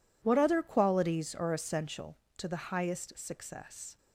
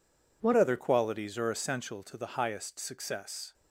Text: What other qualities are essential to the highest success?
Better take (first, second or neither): first